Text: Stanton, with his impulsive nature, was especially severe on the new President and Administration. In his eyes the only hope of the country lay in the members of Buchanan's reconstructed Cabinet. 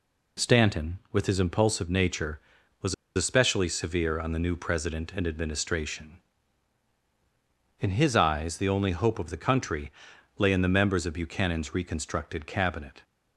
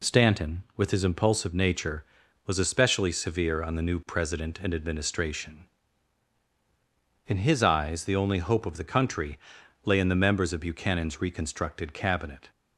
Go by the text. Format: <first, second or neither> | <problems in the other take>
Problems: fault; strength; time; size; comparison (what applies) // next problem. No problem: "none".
second | pauses between "was" and "especially"; slight; at 2.9 s; 0.21 s long // pauses between "country" and "lay"; noticeable; at 9.8 s; 0.48 s long; noticeable in the second